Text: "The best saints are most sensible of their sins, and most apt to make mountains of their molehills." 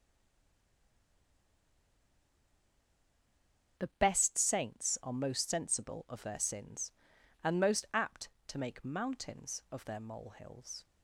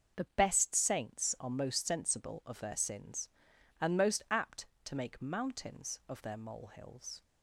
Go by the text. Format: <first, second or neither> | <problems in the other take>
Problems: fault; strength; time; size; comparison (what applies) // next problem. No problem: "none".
second | stays silent before the first word; strong; until 3.7 s; 3.7 s long // starts louder than the rest; until 4.8 s; 6.5 dB; also in the second